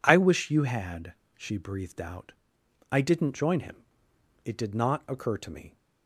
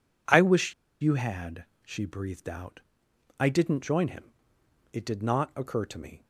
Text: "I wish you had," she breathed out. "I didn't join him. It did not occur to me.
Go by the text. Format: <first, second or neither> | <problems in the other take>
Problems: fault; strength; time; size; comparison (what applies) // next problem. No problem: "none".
first | pauses between "wish" and "you"; slight; at 0.7 s; 0.27 s long